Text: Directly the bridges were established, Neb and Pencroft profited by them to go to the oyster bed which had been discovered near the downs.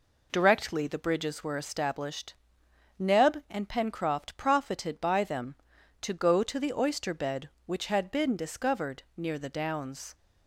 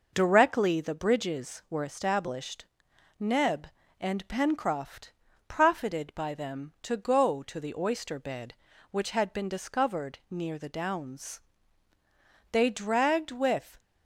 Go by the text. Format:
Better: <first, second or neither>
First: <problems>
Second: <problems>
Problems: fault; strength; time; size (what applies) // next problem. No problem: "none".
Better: first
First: none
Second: pauses between "Pencroft" and "profited"; slight; at 5.1 s; 0.36 s long // goes on to say "They dragged with"; noticeable; from 12.5 s on; 1.2 s long